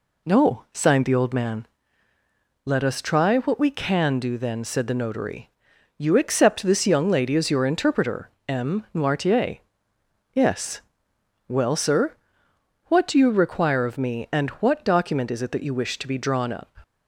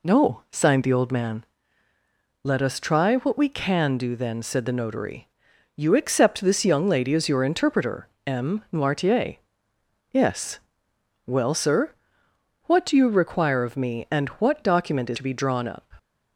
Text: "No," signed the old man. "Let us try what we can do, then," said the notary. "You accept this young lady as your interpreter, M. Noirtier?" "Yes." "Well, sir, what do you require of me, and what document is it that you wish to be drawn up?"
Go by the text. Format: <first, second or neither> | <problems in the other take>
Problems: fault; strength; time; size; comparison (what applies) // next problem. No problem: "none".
first | skips "it that you wish"; at 15.1 s